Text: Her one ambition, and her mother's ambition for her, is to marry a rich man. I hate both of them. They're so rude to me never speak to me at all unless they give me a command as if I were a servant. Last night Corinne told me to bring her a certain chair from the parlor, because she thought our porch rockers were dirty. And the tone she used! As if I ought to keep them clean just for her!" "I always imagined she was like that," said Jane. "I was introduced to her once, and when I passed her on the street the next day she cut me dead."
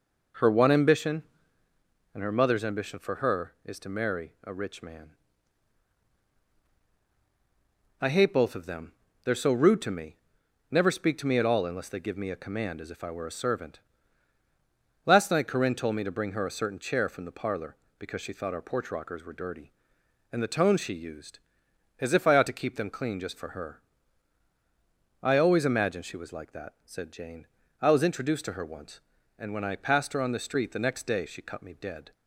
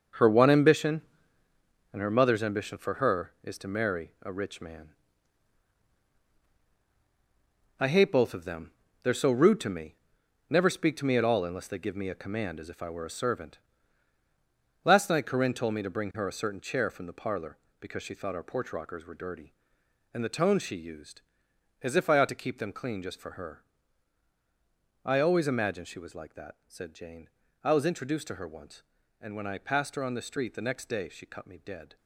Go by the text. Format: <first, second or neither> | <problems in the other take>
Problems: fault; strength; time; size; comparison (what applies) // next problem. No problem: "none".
first | gets quieter; strong; throughout; 9.5 dB // pauses between "me" and "never"; noticeable; at 9.9 s; 0.56 s long; noticeable in the first